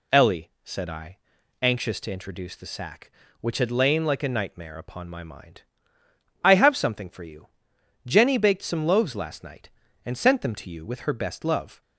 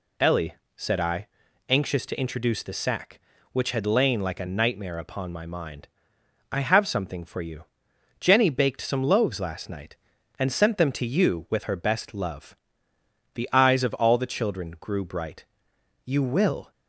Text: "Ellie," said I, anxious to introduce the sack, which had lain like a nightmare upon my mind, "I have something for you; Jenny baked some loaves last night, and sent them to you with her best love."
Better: first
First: none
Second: goes on to say "The eyes of all the children grew bright You will"; strong; from 13.3 s on; 3.3 s long

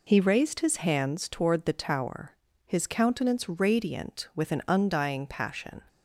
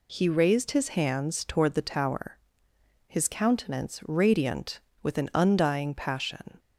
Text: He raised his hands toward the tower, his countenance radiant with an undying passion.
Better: neither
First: none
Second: none

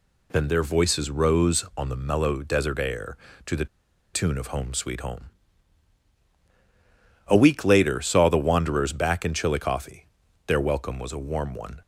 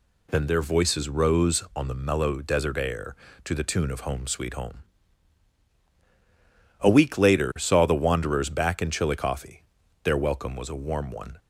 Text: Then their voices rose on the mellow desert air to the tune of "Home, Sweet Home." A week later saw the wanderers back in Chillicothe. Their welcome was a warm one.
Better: second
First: pauses between "the" and "tune"; noticeable; at 3.6 s; 0.48 s long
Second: none

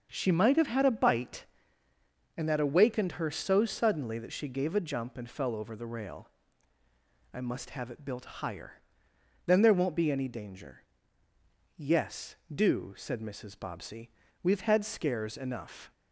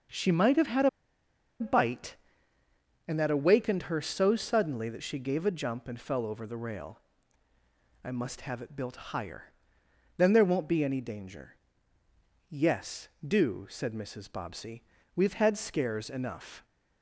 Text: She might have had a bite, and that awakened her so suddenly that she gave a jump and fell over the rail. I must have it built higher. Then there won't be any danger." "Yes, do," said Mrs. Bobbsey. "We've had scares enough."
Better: first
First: starts louder than the rest; until 1.1 s; 6.5 dB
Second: starts louder than the rest; until 1.8 s; 6.5 dB // pauses between "a" and "bite"; noticeable; at 0.8 s; 0.71 s long

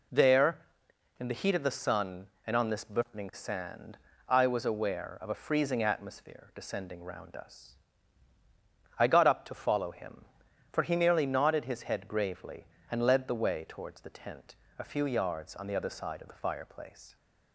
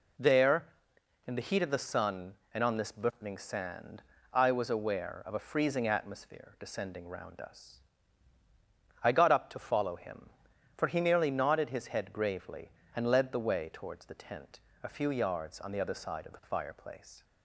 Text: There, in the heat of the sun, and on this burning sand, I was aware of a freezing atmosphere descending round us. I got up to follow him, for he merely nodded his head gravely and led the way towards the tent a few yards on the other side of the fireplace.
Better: neither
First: pauses between "tent" and "a"; slight; at 14.5 s; 0.22 s long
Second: pauses between "tent" and "a"; slight; at 14.6 s; 0.22 s long

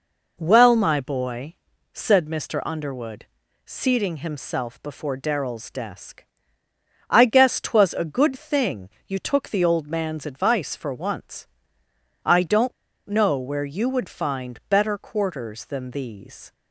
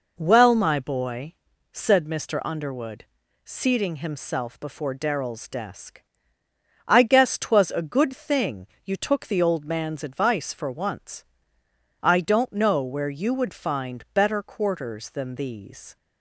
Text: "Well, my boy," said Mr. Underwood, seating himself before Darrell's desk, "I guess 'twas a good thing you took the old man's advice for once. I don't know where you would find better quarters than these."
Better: second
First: pauses between "thing" and "you"; slight; at 8.8 s; 0.18 s long // pauses between "don't" and "know"; slight; at 12.7 s; 0.35 s long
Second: pauses between "thing" and "you"; slight; at 8.6 s; 0.18 s long

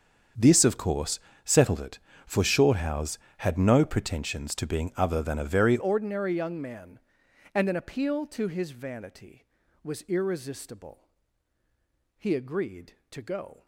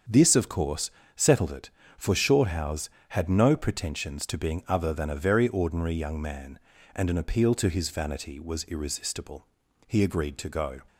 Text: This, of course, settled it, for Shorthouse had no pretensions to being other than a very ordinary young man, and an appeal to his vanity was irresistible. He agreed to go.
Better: second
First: starts louder than the rest; strong; until 1.6 s; 7 dB // changes voice at "ordinary"; from 5.7 s on; 7.9 s long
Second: starts louder than the rest; strong; until 1.3 s; 7.5 dB

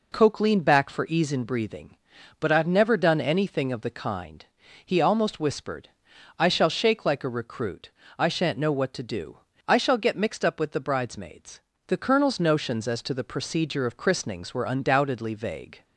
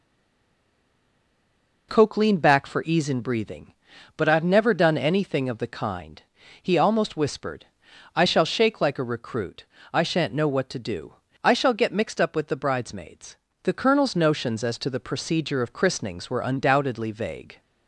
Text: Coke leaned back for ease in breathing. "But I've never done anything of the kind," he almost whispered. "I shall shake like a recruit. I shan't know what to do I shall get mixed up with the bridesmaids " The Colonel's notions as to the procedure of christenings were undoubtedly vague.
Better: first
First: pauses between "do" and "I"; slight; at 9.3 s; 0.32 s long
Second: stays silent before the first word; noticeable; until 1.8 s; 1.8 s long // pauses between "do" and "I"; slight; at 11.1 s; 0.32 s long

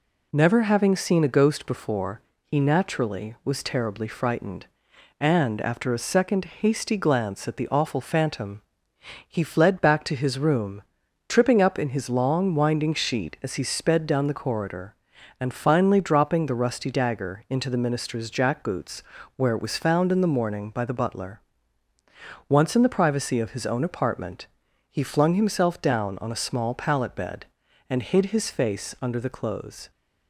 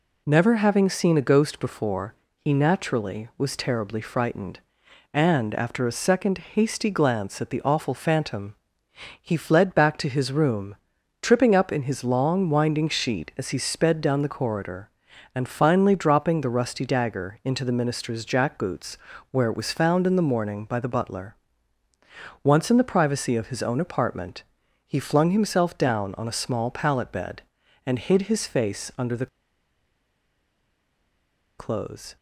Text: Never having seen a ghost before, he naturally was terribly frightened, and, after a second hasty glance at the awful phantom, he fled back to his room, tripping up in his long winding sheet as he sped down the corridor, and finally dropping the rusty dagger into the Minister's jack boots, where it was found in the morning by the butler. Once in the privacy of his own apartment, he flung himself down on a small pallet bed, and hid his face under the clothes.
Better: first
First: pauses between "second" and "hasty"; slight; at 6.4 s; 0.16 s long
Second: pauses between "second" and "hasty"; slight; at 6.3 s; 0.16 s long // pauses between "the" and "clothes"; strong; at 29.2 s; 2.3 s long

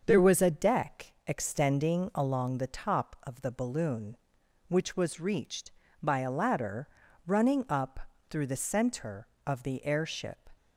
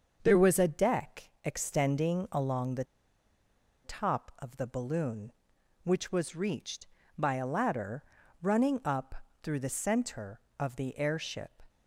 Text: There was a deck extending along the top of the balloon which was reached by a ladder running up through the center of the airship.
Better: first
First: starts louder than the rest; until 1.0 s; 6.5 dB // pauses between "ladder" and "running"; at 6.8 s; 0.38 s long // pauses between "up" and "through"; slight; at 7.9 s; 0.30 s long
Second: starts louder than the rest; until 1.2 s; 6.5 dB // pauses between "the" and "top"; at 2.8 s; 1.0 s long // pauses between "ladder" and "running"; at 8.0 s; 0.38 s long // pauses between "up" and "through"; slight; at 9.1 s; 0.28 s long

